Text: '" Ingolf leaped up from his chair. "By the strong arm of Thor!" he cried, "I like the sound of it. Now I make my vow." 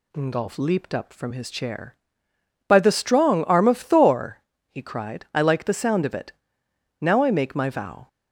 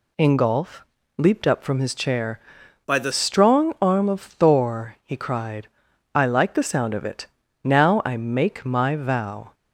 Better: first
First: none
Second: pauses between "Ingolf" and "leaped"; slight; at 0.8 s; 0.34 s long // changes voice from "By" to "the"; from 2.8 to 3.1 s; 0.3 s long

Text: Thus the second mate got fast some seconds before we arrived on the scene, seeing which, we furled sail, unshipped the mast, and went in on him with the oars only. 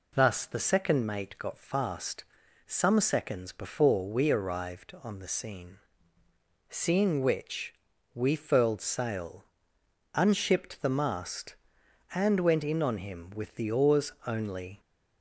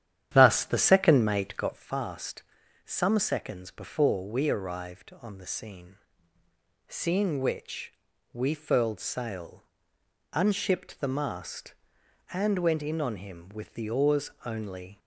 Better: first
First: pauses between "fast" and "some"; at 2.2 s; 0.42 s long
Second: starts louder than the rest; strong; until 1.9 s; 10.5 dB // pauses between "fast" and "some"; at 2.4 s; 0.42 s long

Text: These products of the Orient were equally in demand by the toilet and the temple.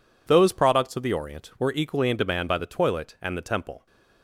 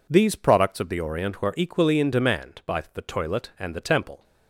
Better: second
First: says "Those" for "These"; at 0.2 s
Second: none

